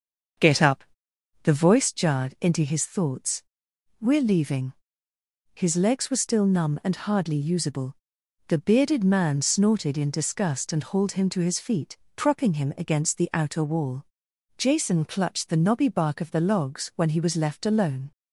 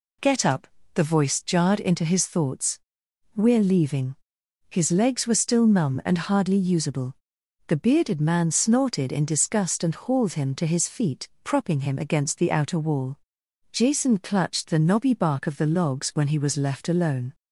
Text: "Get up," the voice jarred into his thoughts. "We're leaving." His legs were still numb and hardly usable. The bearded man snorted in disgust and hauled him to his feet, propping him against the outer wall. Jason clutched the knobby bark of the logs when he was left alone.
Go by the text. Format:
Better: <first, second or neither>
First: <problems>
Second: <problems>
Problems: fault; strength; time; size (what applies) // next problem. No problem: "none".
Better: second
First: starts louder than the rest; until 1.9 s; 6.5 dB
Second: none